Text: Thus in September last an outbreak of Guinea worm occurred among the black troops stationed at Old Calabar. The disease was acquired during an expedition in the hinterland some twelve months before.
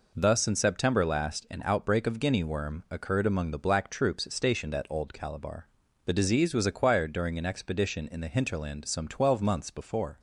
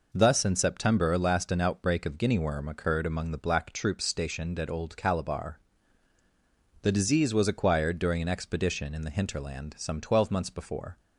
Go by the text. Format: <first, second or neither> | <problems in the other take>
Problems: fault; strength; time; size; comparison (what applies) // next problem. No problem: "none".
neither | none